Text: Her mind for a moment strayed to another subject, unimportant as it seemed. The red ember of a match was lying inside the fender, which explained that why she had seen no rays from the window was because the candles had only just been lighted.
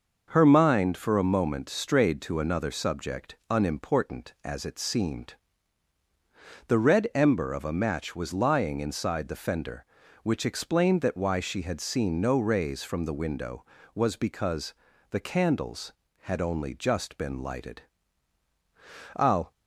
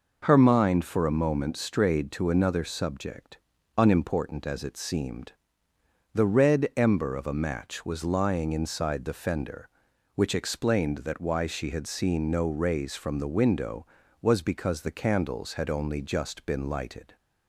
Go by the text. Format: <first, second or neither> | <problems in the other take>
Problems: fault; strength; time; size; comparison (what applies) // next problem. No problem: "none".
second | pauses between "because" and "the"; slight; at 14.7 s; 0.34 s long // goes on to say "I'll"; slight; from 19.1 s on; 0.34 s long